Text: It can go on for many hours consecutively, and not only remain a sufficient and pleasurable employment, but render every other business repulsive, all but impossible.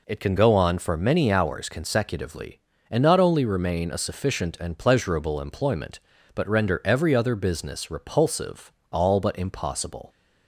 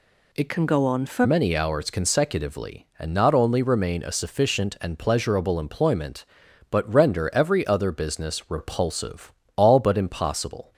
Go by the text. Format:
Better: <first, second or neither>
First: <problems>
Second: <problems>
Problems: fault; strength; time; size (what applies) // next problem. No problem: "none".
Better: first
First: none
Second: changes voice from "can" to "for"; from 0.4 to 1.2 s; 0.8 s long